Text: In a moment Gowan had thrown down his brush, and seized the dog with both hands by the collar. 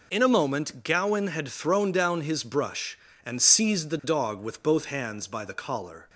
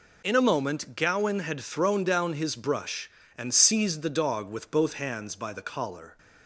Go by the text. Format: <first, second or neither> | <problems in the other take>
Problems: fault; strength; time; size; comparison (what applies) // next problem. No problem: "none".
neither | none